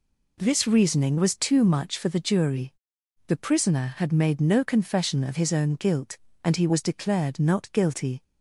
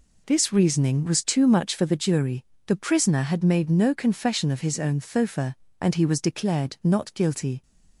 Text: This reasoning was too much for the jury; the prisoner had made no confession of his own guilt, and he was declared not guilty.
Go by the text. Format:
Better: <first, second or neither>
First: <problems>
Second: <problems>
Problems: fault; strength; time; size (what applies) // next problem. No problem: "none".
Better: first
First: none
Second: says "thofa" for "guilt"; at 4.9 s